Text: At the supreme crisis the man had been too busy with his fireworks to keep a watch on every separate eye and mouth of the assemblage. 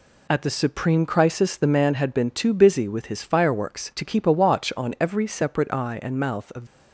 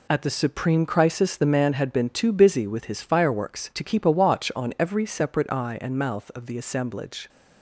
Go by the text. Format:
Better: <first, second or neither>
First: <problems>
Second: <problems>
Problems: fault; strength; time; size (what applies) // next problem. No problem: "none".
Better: second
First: stops before "the assemblage"; at 6.6 s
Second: none